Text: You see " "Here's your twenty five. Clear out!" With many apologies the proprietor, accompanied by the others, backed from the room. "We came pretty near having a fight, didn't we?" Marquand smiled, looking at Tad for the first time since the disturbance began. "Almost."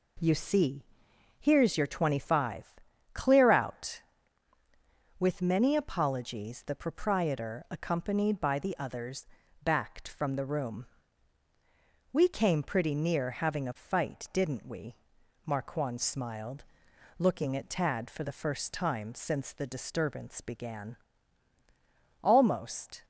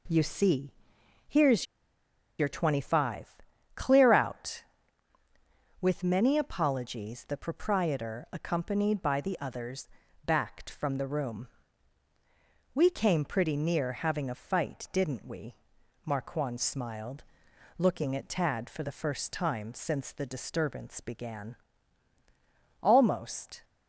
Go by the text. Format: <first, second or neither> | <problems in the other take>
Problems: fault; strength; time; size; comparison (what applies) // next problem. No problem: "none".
first | pauses between "Here's" and "your"; noticeable; at 1.6 s; 0.74 s long